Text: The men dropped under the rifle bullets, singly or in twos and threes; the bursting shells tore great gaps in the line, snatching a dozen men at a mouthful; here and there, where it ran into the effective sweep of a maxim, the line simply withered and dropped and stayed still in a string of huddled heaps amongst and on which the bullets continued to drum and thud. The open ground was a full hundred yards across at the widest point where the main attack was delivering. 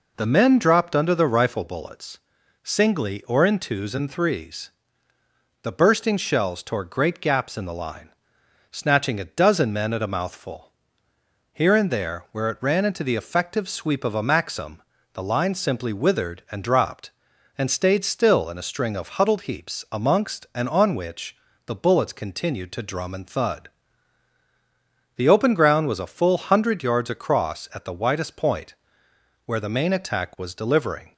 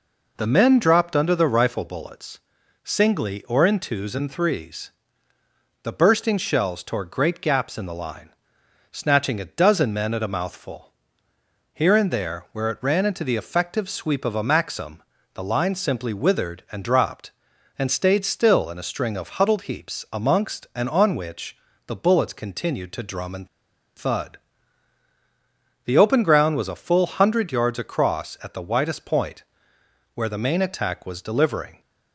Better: first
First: pauses between "which" and "the"; slight; at 21.3 s; 0.30 s long // pauses between "point" and "where"; noticeable; at 28.7 s; 0.70 s long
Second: pauses between "which" and "the"; slight; at 21.5 s; 0.30 s long // pauses between "and" and "thud"; noticeable; at 23.4 s; 0.48 s long // pauses between "point" and "where"; noticeable; at 29.4 s; 0.70 s long

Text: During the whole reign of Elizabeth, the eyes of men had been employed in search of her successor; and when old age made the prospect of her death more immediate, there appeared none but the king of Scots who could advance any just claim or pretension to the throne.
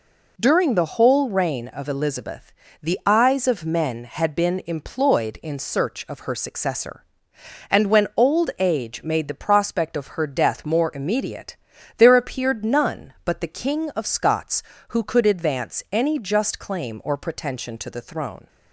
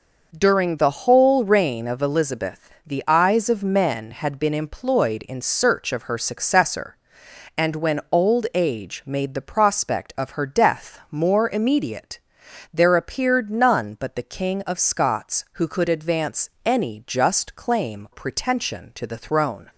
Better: first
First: none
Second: skips "or"; at 18.0 s

